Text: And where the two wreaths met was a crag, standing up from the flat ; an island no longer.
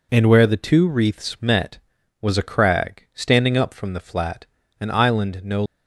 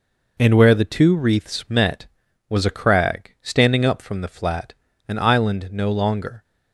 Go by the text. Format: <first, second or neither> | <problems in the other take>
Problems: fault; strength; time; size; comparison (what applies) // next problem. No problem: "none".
second | stops before "longer"; at 5.6 s